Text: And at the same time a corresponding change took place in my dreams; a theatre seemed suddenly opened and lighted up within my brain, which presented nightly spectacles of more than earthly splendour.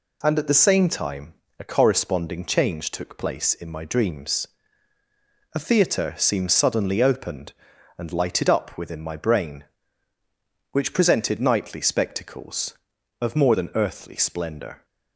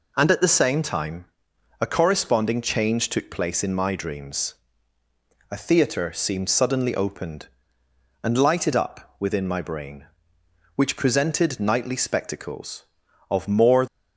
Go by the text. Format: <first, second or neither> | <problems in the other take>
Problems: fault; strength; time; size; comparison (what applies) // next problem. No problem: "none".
first | pauses between "time" and "a"; noticeable; at 1.2 s; 0.54 s long; slight in the first // stops before "than earthly splendour"; at 13.8 s